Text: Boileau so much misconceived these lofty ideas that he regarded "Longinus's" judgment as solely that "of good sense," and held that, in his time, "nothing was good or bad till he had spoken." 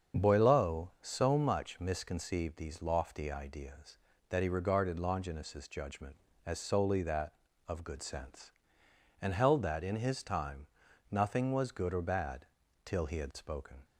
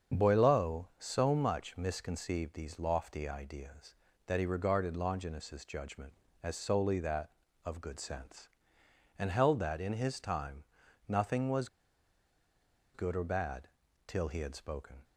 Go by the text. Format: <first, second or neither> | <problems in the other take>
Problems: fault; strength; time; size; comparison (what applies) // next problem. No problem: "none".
first | starts louder than the rest; strong; until 1.2 s; 7 dB; strong in the first // pauses between "was" and "good"; strong; at 11.6 s; 1.2 s long // pauses between "bad" and "till"; at 13.6 s; 0.40 s long; also in the first